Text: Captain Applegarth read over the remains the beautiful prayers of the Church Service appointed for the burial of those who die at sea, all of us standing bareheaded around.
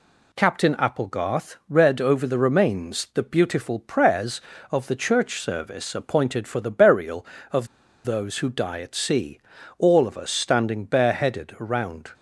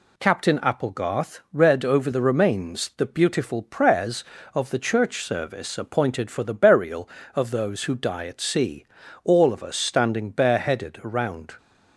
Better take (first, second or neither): second